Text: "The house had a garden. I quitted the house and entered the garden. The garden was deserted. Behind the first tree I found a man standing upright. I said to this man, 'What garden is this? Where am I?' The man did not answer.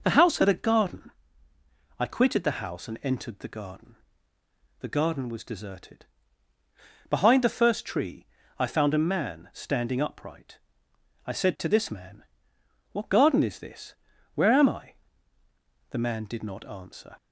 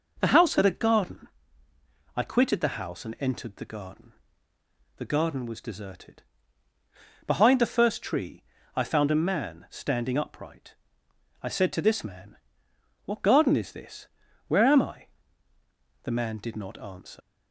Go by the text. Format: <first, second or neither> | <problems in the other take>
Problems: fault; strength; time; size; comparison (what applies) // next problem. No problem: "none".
first | pauses between "tree" and "I"; slight; at 8.4 s; 0.32 s long; slight in the first // leaves "answer" unfinished; at 17.2 s; 90 ms